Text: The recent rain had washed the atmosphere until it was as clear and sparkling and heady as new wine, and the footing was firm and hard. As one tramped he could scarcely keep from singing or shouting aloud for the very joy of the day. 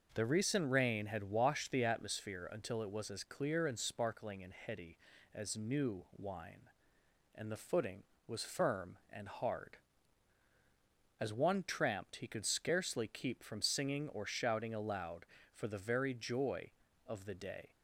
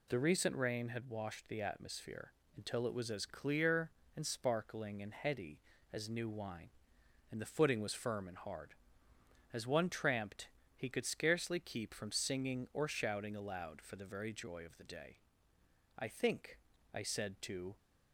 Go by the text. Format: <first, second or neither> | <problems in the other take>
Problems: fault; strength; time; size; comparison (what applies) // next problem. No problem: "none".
first | pauses between "atmosphere" and "until"; slight; at 2.3 s; 0.24 s long // pauses between "tramped" and "he"; slight; at 10.4 s; 0.26 s long // goes on to say "I think I said to"; strong; from 15.9 s on; 1.7 s long